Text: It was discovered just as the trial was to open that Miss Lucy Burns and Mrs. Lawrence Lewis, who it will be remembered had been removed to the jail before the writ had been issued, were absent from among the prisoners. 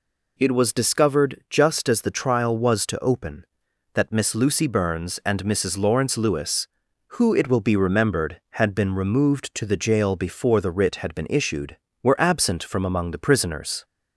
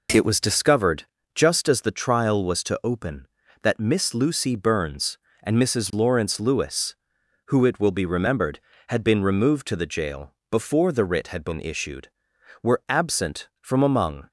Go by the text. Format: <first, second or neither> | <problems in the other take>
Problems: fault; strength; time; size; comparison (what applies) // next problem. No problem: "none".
first | pauses between "discovered" and "just"; slight; at 1.0 s; 0.32 s long // pauses between "jail" and "before"; slight; at 10.3 s; 0.16 s long // stops before "the prisoners"; at 14.2 s